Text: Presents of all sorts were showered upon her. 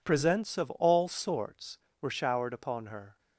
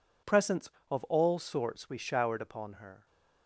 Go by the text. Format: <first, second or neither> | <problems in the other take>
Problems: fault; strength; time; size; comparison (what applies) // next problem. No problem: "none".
first | says "we" for "were"; at 1.8 s